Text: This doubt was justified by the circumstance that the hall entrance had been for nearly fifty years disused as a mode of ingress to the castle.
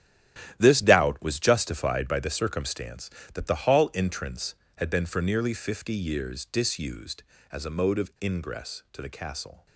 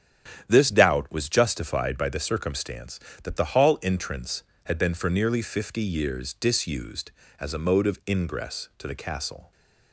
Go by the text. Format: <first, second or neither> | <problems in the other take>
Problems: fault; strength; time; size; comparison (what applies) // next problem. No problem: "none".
second | gets quieter; strong; throughout; 10.5 dB // starts louder than the rest; strong; until 1.5 s; 12 dB; strong in the second